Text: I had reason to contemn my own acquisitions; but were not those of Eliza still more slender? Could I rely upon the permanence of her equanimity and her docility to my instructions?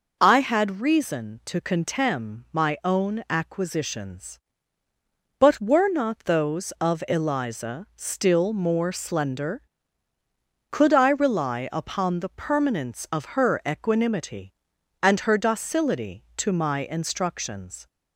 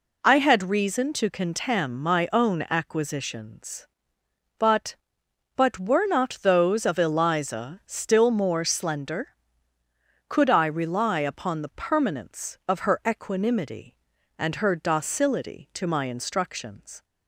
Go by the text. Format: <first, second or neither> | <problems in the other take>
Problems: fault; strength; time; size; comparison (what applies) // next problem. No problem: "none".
first | says "but" twice; at 5.5 s